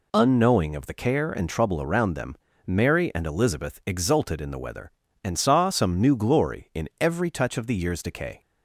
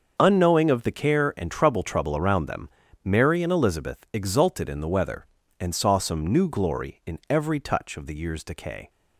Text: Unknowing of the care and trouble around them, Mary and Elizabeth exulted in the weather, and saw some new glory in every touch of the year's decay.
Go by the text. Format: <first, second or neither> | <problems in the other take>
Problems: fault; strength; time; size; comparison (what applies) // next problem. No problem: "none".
first | starts louder than the rest; until 1.1 s; 6.5 dB // says "trouble" twice; at 1.8 s